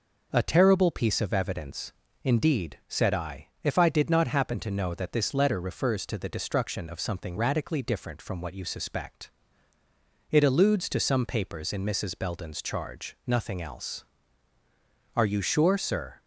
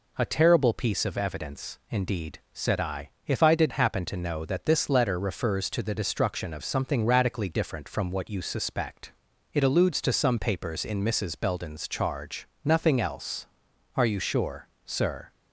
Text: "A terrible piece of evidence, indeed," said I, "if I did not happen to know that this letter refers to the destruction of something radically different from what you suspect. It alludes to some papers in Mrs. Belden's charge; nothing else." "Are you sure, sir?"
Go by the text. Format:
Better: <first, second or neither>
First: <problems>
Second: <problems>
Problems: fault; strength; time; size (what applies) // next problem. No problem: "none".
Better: first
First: none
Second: skips "not"; at 3.7 s